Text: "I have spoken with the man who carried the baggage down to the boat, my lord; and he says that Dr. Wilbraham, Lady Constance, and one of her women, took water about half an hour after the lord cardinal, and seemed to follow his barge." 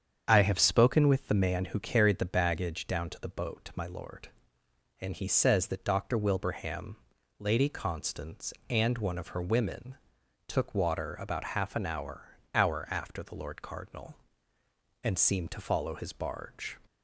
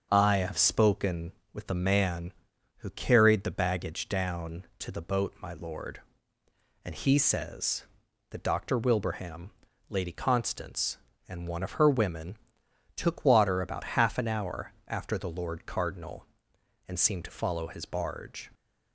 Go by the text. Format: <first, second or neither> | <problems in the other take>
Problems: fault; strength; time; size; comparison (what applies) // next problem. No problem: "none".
second | starts louder than the rest; strong; until 1.2 s; 7.5 dB; also in the second // says "hour" twice; at 12.5 s